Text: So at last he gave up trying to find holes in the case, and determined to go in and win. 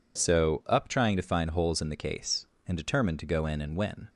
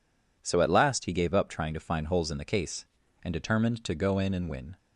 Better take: second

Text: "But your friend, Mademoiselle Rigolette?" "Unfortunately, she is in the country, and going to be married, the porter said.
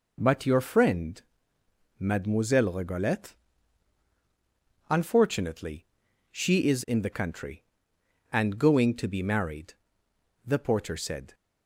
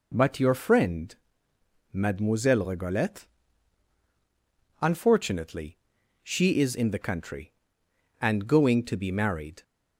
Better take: first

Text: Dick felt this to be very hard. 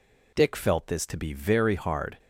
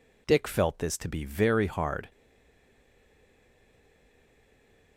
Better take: first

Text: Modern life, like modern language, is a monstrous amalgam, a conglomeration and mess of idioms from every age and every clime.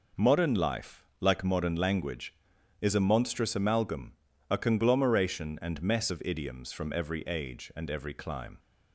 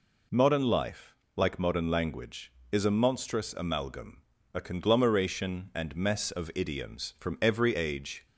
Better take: first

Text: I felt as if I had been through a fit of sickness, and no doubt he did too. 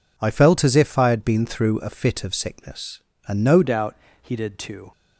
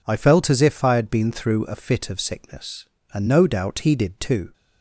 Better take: second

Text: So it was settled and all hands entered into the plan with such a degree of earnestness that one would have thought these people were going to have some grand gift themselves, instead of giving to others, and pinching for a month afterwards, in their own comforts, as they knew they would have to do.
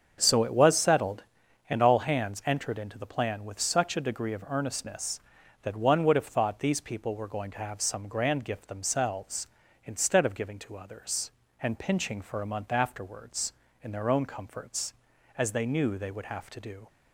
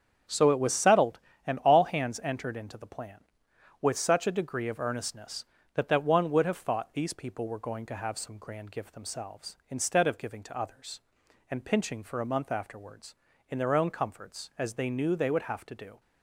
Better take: first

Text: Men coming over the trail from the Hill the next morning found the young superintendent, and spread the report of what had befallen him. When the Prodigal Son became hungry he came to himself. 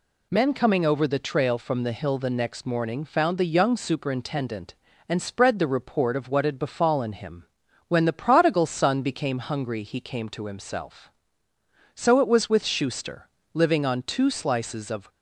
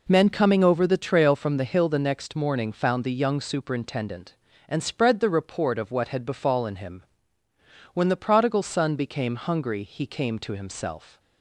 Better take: second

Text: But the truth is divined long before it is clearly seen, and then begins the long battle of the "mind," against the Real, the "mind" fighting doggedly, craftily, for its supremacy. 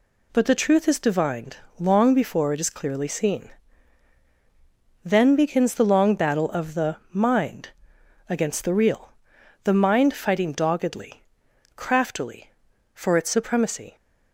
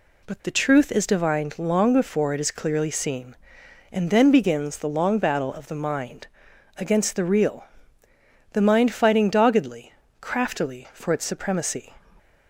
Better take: second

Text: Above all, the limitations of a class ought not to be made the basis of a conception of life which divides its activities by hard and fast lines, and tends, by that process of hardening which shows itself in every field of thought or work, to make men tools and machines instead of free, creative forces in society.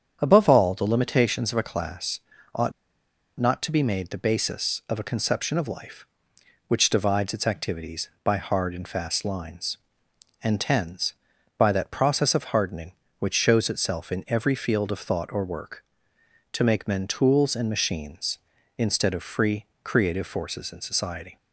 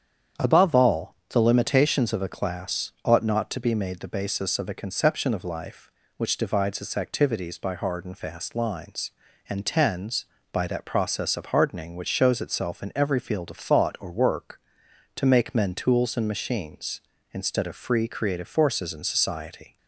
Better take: second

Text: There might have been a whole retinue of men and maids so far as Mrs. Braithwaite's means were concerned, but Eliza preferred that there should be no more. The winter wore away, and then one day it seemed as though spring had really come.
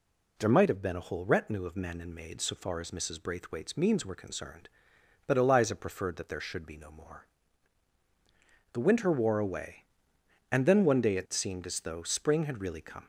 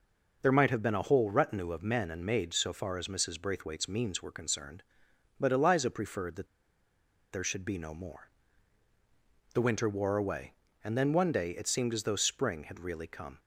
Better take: first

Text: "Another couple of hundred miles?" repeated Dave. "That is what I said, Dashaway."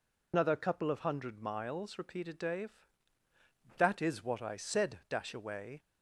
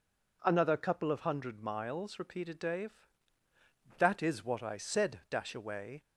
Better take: second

